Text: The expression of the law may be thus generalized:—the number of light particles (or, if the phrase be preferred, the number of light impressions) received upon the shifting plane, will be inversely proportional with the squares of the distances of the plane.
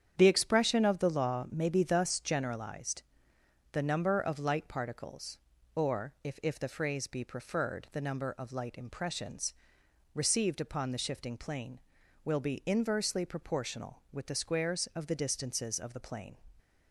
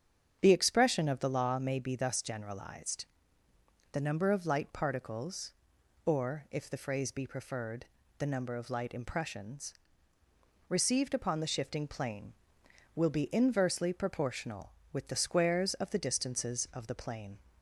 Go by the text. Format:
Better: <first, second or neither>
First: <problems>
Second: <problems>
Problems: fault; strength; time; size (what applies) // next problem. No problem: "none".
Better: second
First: starts louder than the rest; strong; until 1.1 s; 8.5 dB // says "if" twice; at 6.4 s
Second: starts louder than the rest; strong; until 1.4 s; 8 dB